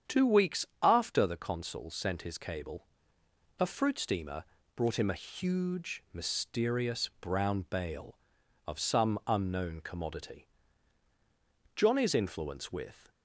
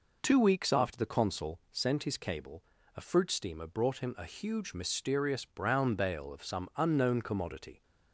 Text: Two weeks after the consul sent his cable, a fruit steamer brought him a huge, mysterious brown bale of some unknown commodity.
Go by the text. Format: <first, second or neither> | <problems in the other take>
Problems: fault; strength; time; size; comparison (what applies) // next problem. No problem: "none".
second | starts louder than the rest; strong; until 1.2 s; 8.5 dB // pauses between "weeks" and "after"; slight; at 0.6 s; 0.18 s long // pauses between "steamer" and "brought"; slight; at 4.4 s; 0.30 s long // goes on to say "Johnny's influence with"; from 11.7 s on; 1.3 s long